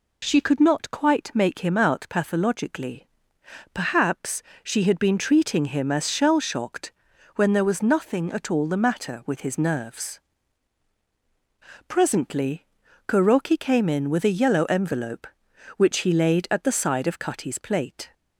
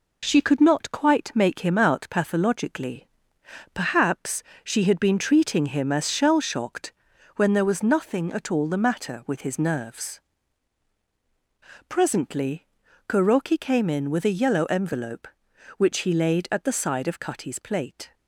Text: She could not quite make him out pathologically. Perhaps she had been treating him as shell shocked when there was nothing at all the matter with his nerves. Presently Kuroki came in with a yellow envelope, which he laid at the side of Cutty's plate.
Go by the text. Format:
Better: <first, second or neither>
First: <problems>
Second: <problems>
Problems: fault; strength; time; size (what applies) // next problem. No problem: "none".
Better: first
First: pauses between "Perhaps" and "she"; slight; at 4.4 s; 0.22 s long // pauses between "shocked" and "when"; at 6.9 s; 0.42 s long // pauses between "Presently" and "Kuroki"; at 12.6 s; 0.40 s long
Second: gets quieter; noticeable; throughout; 4.5 dB // pauses between "Perhaps" and "she"; slight; at 4.4 s; 0.22 s long // pauses between "shocked" and "when"; at 6.9 s; 0.42 s long // pauses between "Presently" and "Kuroki"; at 12.6 s; 0.40 s long